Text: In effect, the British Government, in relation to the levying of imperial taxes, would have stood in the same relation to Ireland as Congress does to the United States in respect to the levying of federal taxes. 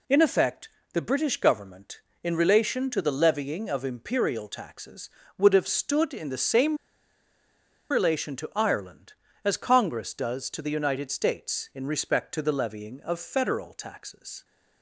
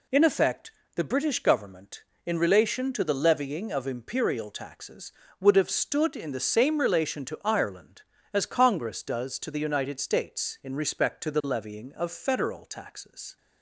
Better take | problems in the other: second | pauses between "same" and "relation"; at 6.7 s; 1.1 s long

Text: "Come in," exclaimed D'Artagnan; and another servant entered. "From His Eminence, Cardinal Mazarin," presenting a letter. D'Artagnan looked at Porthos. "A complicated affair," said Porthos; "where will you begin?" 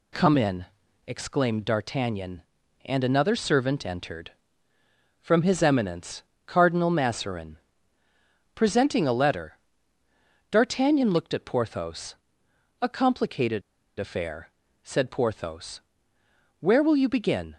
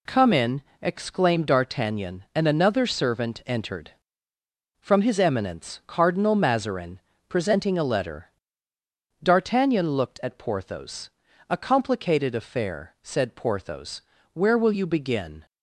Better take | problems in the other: second | pauses between "complicated" and "affair"; at 13.6 s; 0.37 s long

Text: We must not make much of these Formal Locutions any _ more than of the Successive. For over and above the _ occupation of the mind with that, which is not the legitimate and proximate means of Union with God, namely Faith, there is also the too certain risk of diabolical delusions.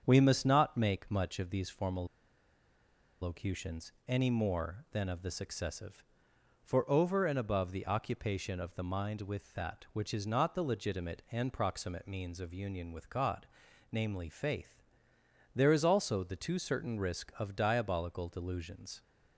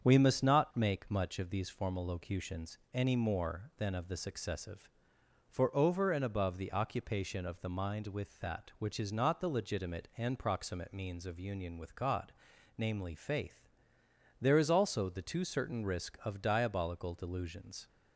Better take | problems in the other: second | starts louder than the rest; strong; until 1.0 s; 7.5 dB; strong in the second // pauses between "Formal" and "Locutions"; at 2.0 s; 1.1 s long // pauses between "Locutions" and "any"; slight; at 3.8 s; 0.18 s long; slight in the second

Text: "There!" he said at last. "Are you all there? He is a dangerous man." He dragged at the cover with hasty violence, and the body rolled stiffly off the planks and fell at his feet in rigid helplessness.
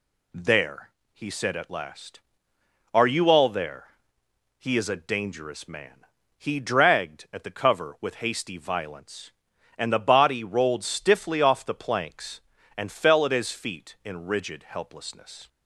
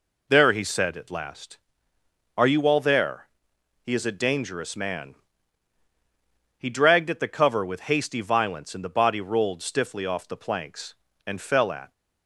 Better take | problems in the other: first | stops before "his feet in rigid helplessness"; at 11.9 s

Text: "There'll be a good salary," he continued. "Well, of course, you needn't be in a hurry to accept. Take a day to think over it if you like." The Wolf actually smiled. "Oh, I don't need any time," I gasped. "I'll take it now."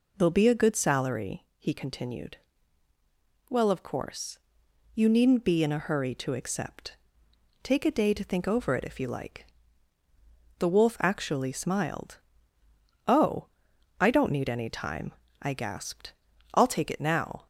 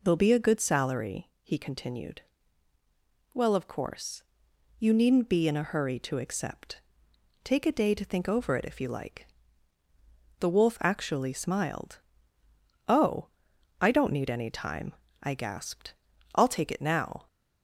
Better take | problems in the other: neither | none

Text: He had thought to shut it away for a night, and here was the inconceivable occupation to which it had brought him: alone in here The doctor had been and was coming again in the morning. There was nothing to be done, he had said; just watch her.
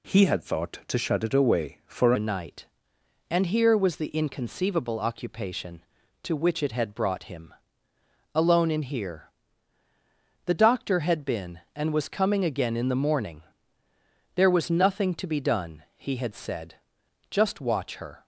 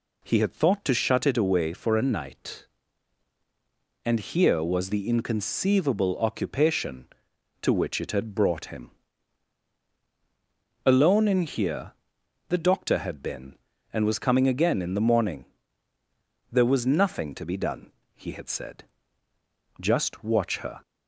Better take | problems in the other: second | changes voice at "a"; from 2.1 s on; 16.1 s long // pauses between "here" and "The"; at 9.2 s; 1.1 s long; noticeable in the second

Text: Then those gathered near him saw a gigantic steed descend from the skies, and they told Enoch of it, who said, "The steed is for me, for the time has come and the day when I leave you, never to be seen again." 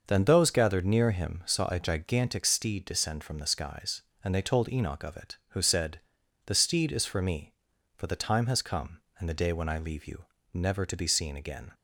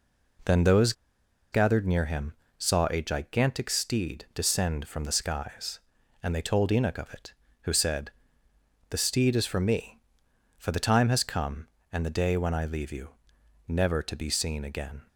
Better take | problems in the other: first | pauses between "those" and "gathered"; noticeable; at 0.9 s; 0.60 s long // pauses between "him" and "saw"; slight; at 2.3 s; 0.24 s long

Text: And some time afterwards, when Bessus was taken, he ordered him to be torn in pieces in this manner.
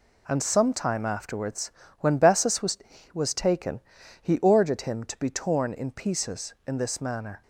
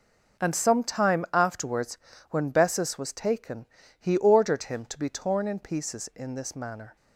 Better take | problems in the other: second | says "was" twice; at 3.1 s

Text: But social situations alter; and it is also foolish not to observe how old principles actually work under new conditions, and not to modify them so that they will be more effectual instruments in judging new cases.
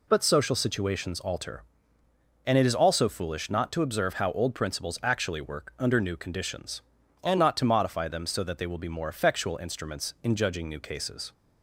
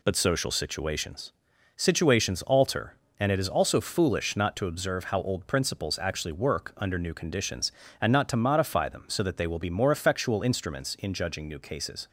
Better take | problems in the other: first | says "situations" twice; at 1.7 s

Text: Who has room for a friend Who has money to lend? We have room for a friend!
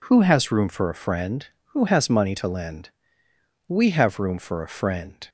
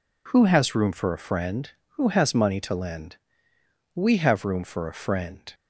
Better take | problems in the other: neither | none

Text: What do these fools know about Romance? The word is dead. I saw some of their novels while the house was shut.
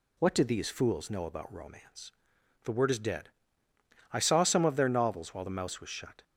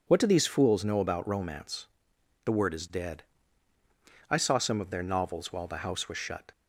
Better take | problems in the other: second | says "mouse" for "house"; at 5.5 s

